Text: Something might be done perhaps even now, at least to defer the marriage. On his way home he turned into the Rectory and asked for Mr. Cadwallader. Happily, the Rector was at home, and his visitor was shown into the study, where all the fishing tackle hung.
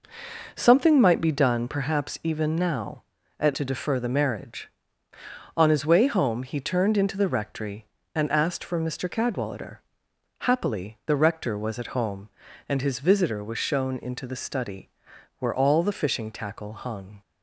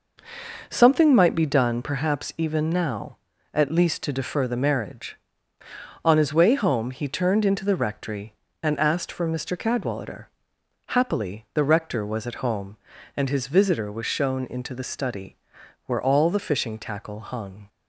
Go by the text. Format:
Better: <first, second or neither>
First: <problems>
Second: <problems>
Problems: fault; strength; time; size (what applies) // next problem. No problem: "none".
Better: second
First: skips "least"; at 3.5 s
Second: none